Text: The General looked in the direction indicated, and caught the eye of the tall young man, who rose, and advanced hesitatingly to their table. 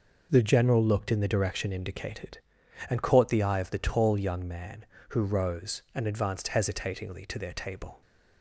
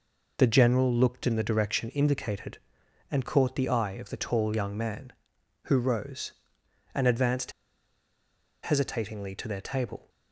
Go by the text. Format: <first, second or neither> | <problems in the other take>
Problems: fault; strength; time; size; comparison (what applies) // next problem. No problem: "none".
first | pauses between "advanced" and "hesitatingly"; at 7.5 s; 1.1 s long